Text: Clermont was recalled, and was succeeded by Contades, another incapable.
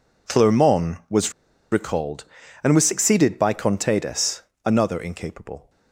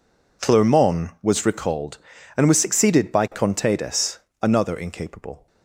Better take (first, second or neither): second